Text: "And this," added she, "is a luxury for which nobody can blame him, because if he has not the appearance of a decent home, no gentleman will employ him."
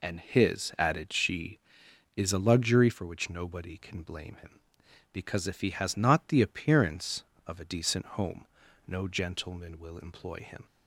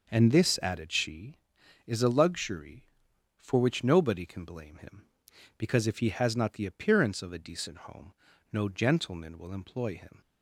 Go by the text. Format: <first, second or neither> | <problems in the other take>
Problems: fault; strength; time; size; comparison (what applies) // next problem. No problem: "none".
second | says "his" for "this"; at 0.2 s